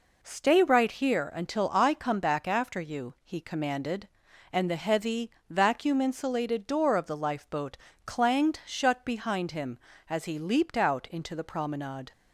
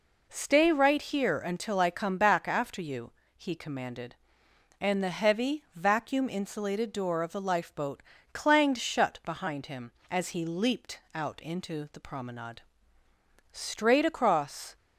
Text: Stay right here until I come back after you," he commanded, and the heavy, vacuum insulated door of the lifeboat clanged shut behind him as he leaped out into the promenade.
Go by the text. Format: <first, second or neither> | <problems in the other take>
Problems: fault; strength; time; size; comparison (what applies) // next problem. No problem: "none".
first | pauses between "lifeboat" and "clanged"; slight; at 8.0 s; 0.32 s long; slight in the first // goes on to say "Straight across"; noticeable; from 13.5 s on; 1.2 s long